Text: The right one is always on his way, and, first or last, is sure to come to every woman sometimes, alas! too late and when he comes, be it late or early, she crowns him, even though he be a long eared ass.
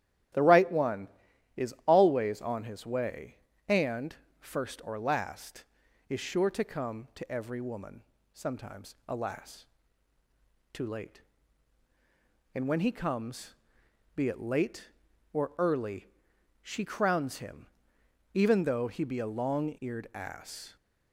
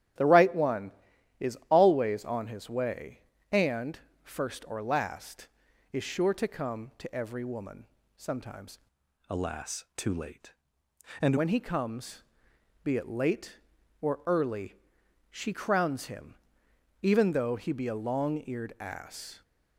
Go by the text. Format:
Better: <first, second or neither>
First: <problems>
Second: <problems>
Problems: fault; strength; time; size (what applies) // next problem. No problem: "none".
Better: first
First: starts louder than the rest; strong; until 1.9 s; 12 dB // pauses between "woman" and "sometimes"; slight; at 8.0 s; 0.32 s long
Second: starts louder than the rest; strong; until 1.7 s; 11.5 dB // pauses between "woman" and "sometimes"; slight; at 7.8 s; 0.32 s long // changes voice from "alas" to "and"; from 9.2 to 11.3 s; 2.1 s long